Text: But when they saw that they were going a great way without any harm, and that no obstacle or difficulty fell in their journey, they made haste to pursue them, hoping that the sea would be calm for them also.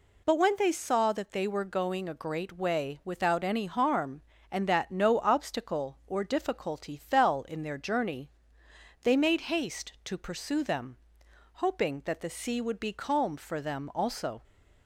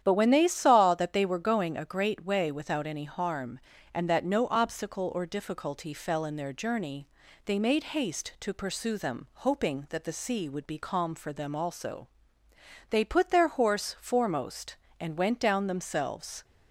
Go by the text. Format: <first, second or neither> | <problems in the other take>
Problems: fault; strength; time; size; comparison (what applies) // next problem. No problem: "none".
first | starts louder than the rest; strong; until 1.0 s; 9.5 dB // goes on to say "They put their horse foremost and went down themselves"; strong; from 12.8 s on; 3.5 s long